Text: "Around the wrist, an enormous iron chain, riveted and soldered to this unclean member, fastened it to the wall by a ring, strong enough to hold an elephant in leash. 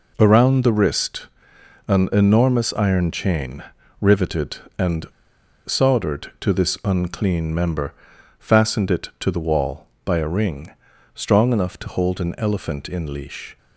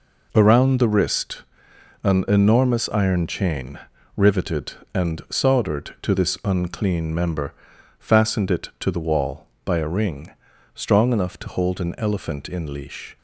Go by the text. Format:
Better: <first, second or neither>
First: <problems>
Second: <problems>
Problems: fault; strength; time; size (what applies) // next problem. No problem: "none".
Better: second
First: pauses between "and" and "soldered"; noticeable; at 5.0 s; 0.58 s long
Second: none